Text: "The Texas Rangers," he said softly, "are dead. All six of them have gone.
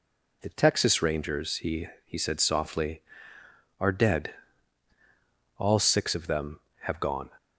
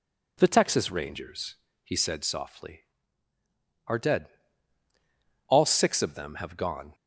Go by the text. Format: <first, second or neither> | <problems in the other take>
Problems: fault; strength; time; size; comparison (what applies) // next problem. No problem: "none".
second | says "he" twice; at 2.0 s